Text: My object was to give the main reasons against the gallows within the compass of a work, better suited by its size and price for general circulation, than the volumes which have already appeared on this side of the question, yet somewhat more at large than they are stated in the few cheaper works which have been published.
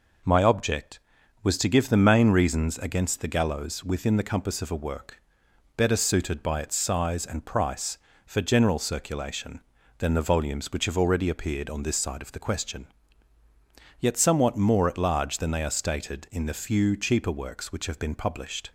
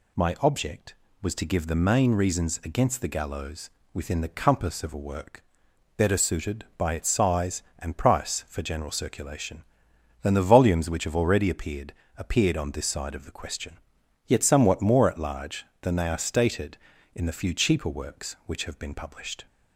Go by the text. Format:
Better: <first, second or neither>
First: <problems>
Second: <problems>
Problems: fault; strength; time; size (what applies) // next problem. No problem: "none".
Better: first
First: none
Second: pauses between "gallows" and "within"; slight; at 3.6 s; 0.24 s long // says "appeared" twice; at 12.1 s